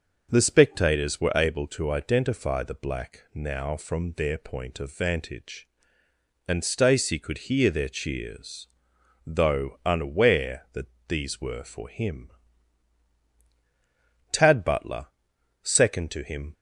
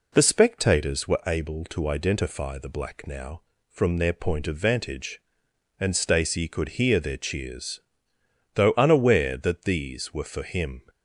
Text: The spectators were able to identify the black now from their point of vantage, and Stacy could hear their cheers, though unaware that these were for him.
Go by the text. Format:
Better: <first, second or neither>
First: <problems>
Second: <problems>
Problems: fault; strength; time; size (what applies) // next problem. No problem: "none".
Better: second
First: starts louder than the rest; until 1.3 s; 6 dB // pauses between "that" and "these"; slight; at 10.8 s; 0.22 s long // goes on to say "Tad Butler second to him"; strong; from 14.2 s on; 2.2 s long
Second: none